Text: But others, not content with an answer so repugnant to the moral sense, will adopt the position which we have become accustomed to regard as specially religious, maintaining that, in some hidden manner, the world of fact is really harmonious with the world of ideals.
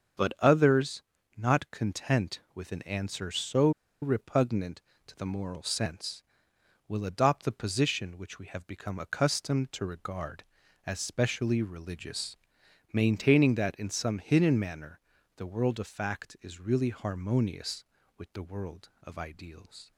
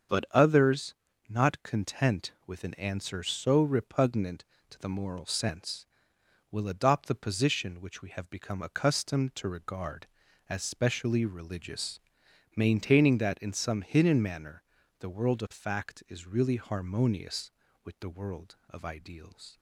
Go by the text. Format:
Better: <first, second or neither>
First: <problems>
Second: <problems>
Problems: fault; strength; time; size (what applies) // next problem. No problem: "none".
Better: second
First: starts louder than the rest; strong; until 1.5 s; 7 dB // pauses between "so" and "repugnant"; slight; at 3.6 s; 0.31 s long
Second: starts louder than the rest; strong; until 1.5 s; 7 dB